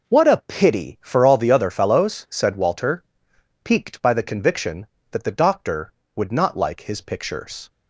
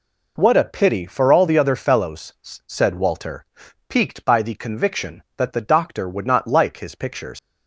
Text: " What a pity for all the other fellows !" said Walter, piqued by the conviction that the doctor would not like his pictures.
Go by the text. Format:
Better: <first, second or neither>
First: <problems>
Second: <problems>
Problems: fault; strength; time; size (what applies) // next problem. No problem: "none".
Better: first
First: none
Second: leaves "pictures" unfinished; at 7.3 s; 135 ms